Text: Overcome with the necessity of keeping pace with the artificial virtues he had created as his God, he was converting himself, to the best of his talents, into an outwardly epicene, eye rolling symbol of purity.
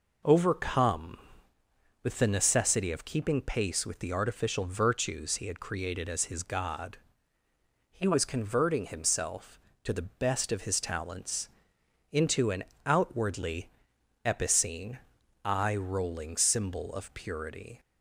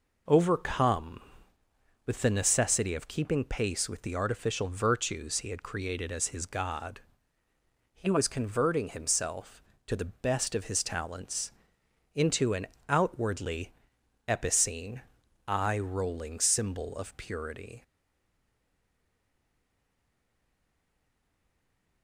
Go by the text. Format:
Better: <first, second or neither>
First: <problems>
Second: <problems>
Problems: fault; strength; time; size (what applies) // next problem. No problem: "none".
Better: first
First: pauses between "an" and "outwardly"; slight; at 12.6 s; 0.22 s long // pauses between "outwardly" and "epicene"; noticeable; at 13.6 s; 0.56 s long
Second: pauses between "an" and "outwardly"; slight; at 12.6 s; 0.22 s long // pauses between "outwardly" and "epicene"; noticeable; at 13.7 s; 0.56 s long // stays silent after the last word; strong; from 17.8 s on; 4.2 s long